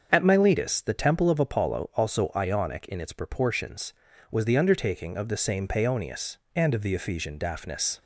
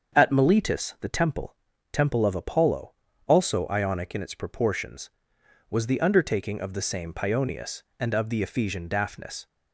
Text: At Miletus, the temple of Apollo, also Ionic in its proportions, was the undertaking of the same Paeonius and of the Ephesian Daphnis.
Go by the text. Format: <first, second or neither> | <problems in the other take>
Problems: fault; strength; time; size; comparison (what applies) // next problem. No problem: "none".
first | starts louder than the rest; until 1.2 s; 7 dB; also in the first // says "temple" twice; at 1.9 s